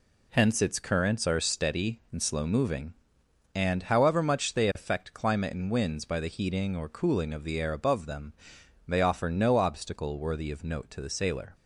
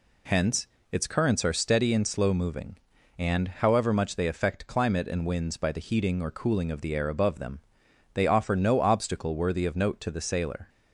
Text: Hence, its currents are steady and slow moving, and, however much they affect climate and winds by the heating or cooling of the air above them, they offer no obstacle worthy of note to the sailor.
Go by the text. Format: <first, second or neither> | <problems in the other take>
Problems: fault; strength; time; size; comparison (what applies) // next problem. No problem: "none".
neither | none